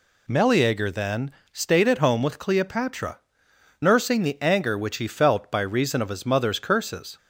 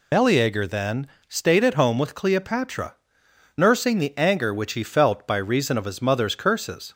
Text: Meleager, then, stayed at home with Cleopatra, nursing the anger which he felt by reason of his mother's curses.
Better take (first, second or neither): first